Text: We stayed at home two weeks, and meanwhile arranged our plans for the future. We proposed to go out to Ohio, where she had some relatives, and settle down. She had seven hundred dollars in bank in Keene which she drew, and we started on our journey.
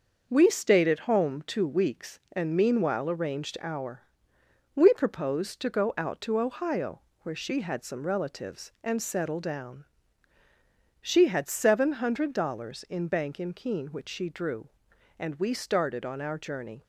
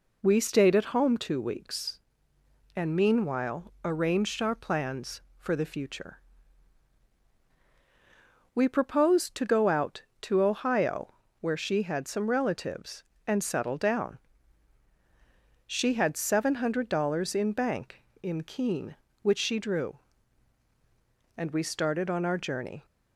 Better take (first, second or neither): second